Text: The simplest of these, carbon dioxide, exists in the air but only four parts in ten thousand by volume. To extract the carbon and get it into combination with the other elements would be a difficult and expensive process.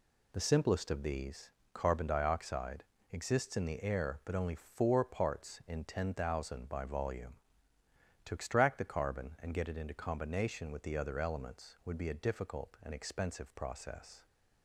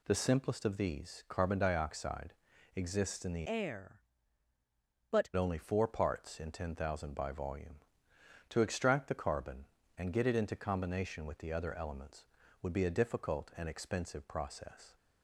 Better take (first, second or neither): first